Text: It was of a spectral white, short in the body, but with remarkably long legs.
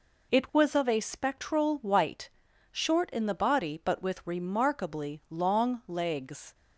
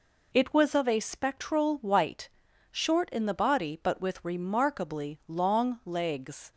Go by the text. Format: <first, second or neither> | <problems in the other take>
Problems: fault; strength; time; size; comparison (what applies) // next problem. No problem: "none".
neither | none